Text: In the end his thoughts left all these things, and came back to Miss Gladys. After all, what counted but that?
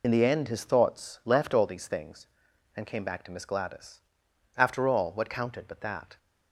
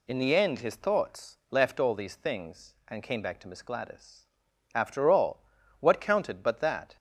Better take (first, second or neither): second